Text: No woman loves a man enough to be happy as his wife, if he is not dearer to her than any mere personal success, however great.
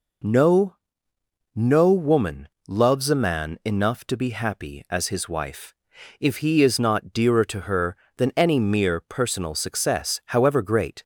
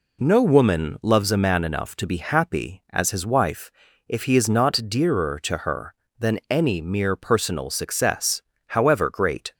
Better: second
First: says "No" twice; at 1.5 s // pauses between "woman" and "loves"; slight; at 2.4 s; 0.22 s long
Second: none

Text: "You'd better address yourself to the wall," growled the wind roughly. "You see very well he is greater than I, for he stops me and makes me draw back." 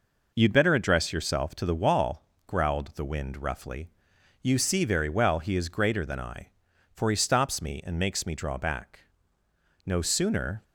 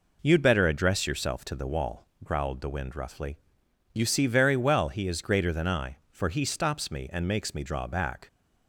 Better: second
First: goes on to say "No sooner"; noticeable; from 9.8 s on; 0.78 s long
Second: none

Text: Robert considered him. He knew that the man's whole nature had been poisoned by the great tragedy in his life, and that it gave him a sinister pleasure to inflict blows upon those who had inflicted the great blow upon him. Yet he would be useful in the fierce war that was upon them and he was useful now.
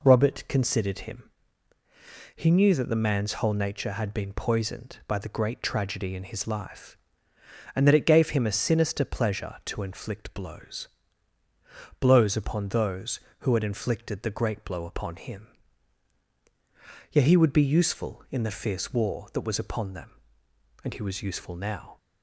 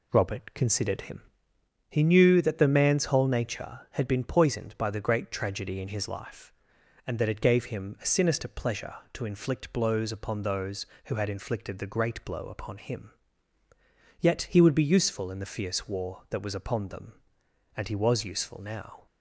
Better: second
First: says "blows" twice; at 11.9 s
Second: none

